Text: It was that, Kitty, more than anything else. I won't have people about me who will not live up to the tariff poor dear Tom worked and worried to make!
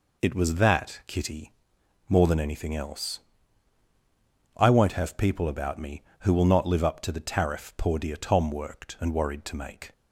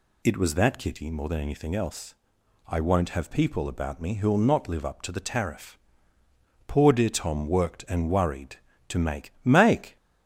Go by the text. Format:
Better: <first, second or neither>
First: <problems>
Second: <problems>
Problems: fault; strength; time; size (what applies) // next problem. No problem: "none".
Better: first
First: none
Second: pauses between "tariff" and "poor"; noticeable; at 5.7 s; 0.92 s long // says "make" twice; at 9.4 s